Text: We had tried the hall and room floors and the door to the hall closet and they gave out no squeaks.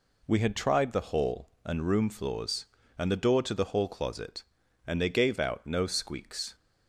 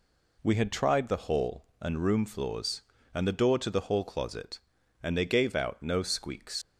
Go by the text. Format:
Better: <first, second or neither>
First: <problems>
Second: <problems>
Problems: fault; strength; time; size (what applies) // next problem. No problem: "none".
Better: first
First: none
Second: leaves "squeaks" unfinished; at 6.6 s; 95 ms